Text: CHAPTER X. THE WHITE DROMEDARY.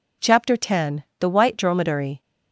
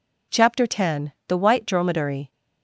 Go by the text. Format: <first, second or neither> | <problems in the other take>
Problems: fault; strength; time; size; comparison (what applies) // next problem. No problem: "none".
neither | none